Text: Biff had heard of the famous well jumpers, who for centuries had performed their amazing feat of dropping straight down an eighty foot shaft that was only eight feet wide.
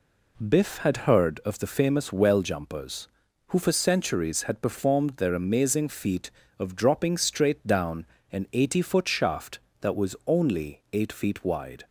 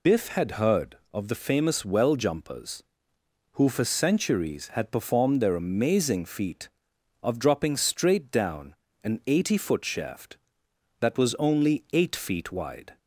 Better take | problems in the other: first | loses the start of "Biff"; at 0.0 s; 175 ms // pauses between "down" and "an"; slight; at 8.7 s; 0.26 s long; slight in the first

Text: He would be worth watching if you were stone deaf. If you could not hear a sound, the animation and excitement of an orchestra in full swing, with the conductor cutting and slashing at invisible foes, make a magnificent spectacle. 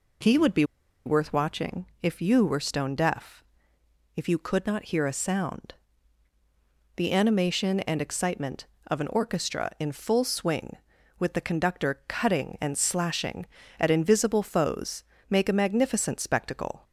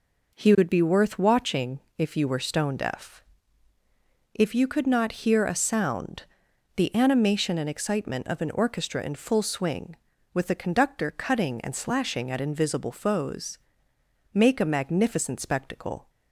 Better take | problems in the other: second | pauses between "be" and "worth"; at 0.6 s; 0.42 s long // pauses between "watching" and "if"; slight; at 1.8 s; 0.16 s long; slight in the second

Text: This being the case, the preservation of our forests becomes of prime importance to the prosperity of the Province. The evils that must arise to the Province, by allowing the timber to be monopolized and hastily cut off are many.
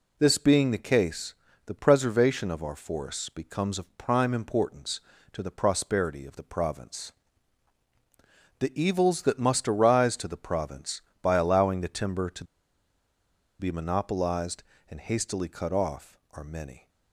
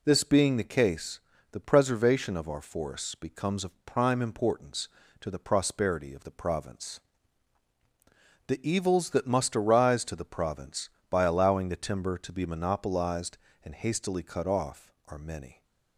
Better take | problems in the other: second | pauses between "to" and "be"; at 12.4 s; 1.1 s long

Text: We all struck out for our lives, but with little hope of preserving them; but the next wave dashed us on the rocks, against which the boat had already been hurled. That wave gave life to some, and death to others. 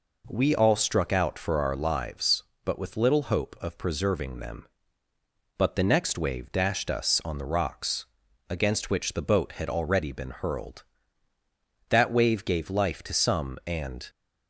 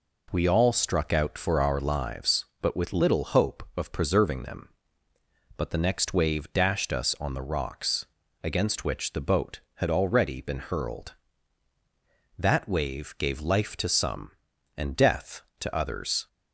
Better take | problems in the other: second | stops before "death to others"; at 14.0 s

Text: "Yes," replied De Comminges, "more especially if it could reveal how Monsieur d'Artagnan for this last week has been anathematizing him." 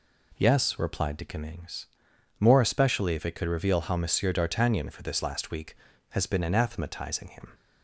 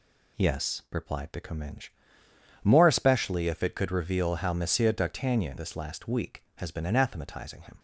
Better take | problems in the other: first | skips "for"; at 5.5 s

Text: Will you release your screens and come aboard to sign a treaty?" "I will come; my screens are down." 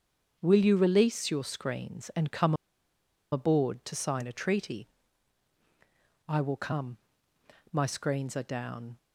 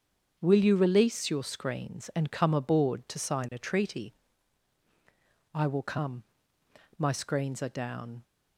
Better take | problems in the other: second | starts louder than the rest; until 1.4 s; 7 dB; strong in the second // pauses between "come" and "aboard"; noticeable; at 2.5 s; 0.78 s long

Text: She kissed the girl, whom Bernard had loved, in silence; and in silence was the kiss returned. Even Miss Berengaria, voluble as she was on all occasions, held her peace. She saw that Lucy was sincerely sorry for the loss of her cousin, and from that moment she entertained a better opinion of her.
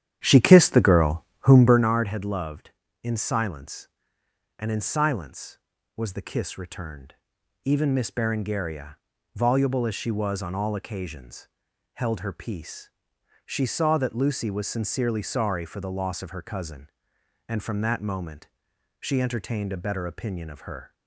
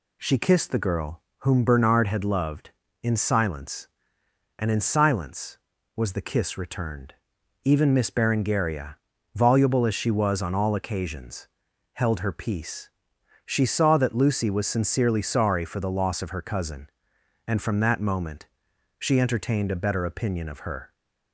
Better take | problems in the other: second | starts louder than the rest; strong; until 1.9 s; 10 dB // pauses between "moment" and "she"; noticeable; at 18.4 s; 0.52 s long; noticeable in the second

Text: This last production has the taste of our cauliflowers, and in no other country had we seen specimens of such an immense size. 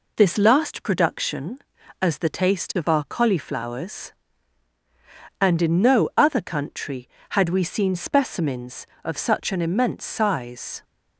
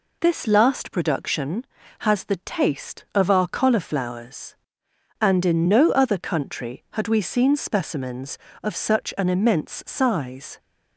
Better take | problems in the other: second | says "as" for "has"; at 2.0 s

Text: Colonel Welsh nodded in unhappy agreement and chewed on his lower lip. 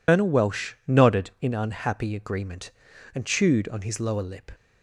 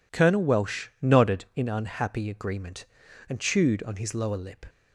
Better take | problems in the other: second | loses the start of "Colonel"; at 0.0 s; 115 ms // pauses between "Welsh" and "nodded"; slight; at 0.7 s; 0.16 s long; slight in the second

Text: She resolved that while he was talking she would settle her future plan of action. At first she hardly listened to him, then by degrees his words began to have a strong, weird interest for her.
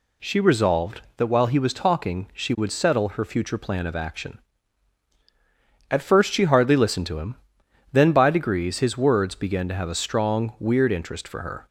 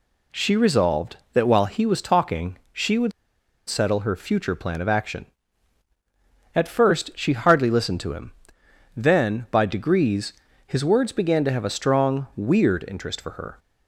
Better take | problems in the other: first | pauses between "would" and "settle"; noticeable; at 3.1 s; 0.56 s long // pauses between "degrees" and "his"; slight; at 10.3 s; 0.32 s long

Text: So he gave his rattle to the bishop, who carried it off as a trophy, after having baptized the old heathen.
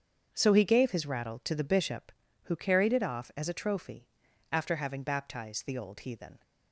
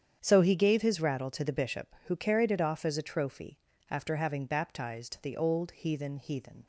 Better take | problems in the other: first | starts louder than the rest; strong; until 1.2 s; 8.5 dB; strong in the first // says "heathen" twice; at 6.1 s

